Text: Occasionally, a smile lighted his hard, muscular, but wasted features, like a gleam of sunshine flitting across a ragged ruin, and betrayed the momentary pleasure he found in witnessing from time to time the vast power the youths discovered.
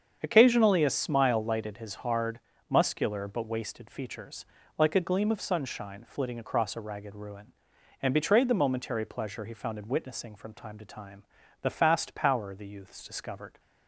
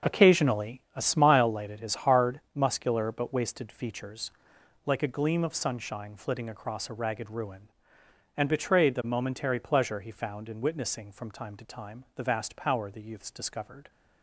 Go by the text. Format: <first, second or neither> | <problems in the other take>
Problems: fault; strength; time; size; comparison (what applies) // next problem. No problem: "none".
second | starts louder than the rest; strong; until 1.2 s; 7.5 dB; also in the second // pauses between "time" and "the"; at 11.2 s; 0.38 s long // says "fast" for "vast"; at 11.7 s